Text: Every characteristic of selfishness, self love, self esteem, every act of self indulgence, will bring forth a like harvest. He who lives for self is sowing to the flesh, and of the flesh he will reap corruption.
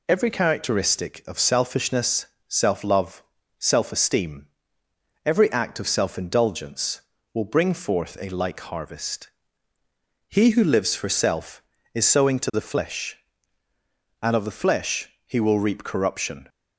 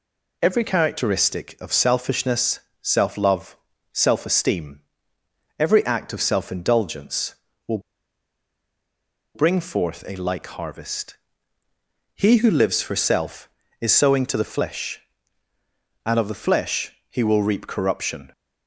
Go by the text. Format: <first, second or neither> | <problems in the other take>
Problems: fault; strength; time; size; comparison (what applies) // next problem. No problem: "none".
first | pauses between "will" and "bring"; strong; at 7.7 s; 1.5 s long // pauses between "flesh" and "he"; slight; at 16.9 s; 0.18 s long; slight in the first